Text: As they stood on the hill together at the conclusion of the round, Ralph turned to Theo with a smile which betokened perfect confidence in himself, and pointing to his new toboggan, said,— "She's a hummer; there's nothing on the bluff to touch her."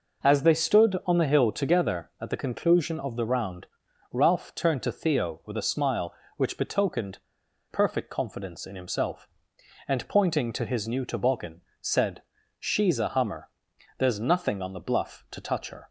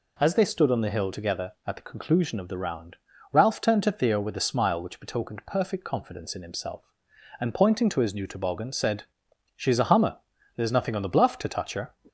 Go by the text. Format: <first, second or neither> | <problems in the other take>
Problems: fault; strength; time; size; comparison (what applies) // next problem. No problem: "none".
second | pauses between "betokened" and "perfect"; noticeable; at 7.1 s; 0.53 s long